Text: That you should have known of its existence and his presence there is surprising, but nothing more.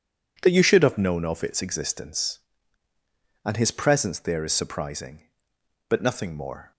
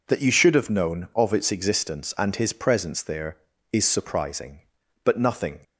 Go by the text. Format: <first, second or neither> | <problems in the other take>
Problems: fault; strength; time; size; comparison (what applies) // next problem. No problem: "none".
first | stops before "more"; at 5.6 s